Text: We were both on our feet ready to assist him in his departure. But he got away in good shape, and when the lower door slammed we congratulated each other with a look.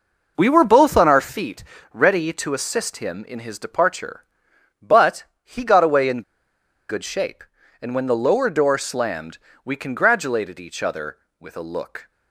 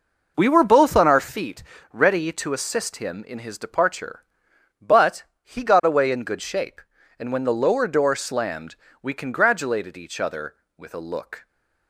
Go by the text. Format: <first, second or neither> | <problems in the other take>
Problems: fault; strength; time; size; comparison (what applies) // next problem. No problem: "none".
second | pauses between "feet" and "ready"; slight; at 1.6 s; 0.30 s long; slight in the second // pauses between "But" and "he"; slight; at 5.2 s; 0.20 s long; slight in the second // pauses between "in" and "good"; noticeable; at 6.2 s; 0.68 s long // pauses between "slammed" and "we"; slight; at 9.3 s; 0.26 s long; slight in the second